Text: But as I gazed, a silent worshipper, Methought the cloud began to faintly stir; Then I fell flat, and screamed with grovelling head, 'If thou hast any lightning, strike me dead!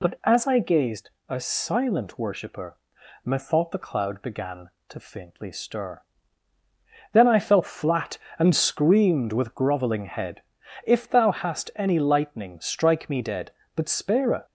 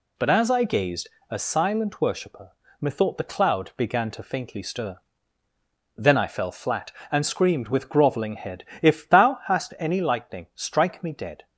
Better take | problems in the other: second | goes on to say "But spare a"; noticeable; from 13.7 s on; 0.70 s long

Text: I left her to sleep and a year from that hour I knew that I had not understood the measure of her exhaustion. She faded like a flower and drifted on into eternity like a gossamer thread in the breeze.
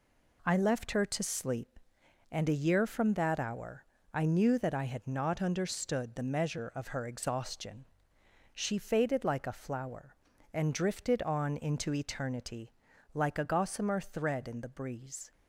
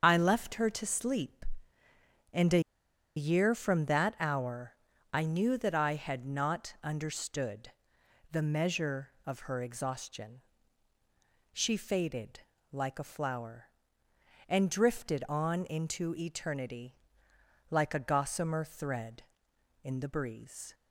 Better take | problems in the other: first | starts louder than the rest; until 1.0 s; 7 dB // pauses between "a" and "year"; noticeable; at 2.6 s; 0.56 s long // pauses between "hour" and "I"; at 4.7 s; 0.40 s long; slight in the first // pauses between "understood" and "the"; noticeable; at 7.6 s; 0.62 s long // pauses between "faded" and "like"; slight; at 12.3 s; 0.32 s long // pauses between "eternity" and "like"; noticeable; at 16.9 s; 0.74 s long; also in the first

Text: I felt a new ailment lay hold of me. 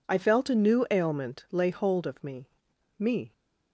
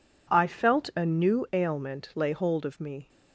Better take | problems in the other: second | says "me" twice; at 2.9 s

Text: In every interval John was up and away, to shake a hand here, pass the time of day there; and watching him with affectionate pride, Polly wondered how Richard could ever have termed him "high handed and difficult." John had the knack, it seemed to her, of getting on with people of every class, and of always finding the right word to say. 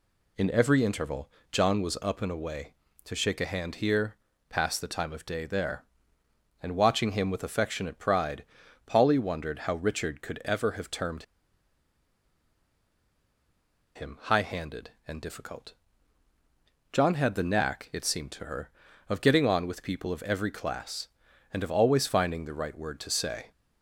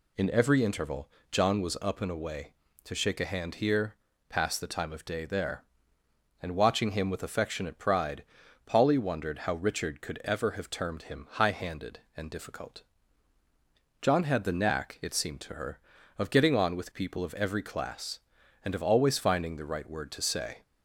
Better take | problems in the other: second | pauses between "interval" and "John"; slight; at 1.3 s; 0.22 s long; slight in the second // pauses between "termed" and "him"; strong; at 11.2 s; 2.7 s long

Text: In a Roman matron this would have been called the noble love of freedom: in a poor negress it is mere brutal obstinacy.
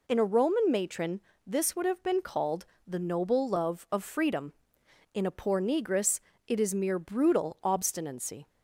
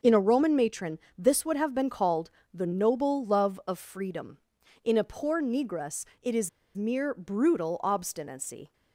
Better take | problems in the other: first | pauses between "matron" and "this"; slight; at 0.9 s; 0.18 s long; slight in the first // pauses between "called" and "the"; slight; at 2.3 s; 0.20 s long; slight in the first // pauses between "negress" and "it"; slight; at 6.0 s; 0.18 s long; slight in the first // pauses between "is" and "mere"; slight; at 6.4 s; 0.27 s long

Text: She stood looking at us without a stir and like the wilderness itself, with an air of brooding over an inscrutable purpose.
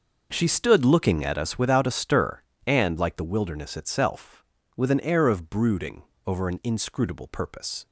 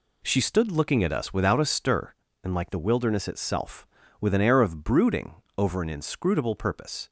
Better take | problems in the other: neither | pauses between "brooding" and "over"; slight; the same in both

